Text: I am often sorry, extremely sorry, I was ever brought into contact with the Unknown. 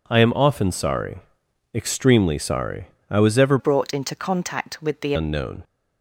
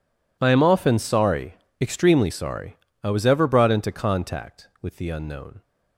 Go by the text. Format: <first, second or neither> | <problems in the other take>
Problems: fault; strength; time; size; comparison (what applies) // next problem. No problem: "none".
second | changes voice from "brought" to "the"; from 3.5 to 5.1 s; 1.6 s long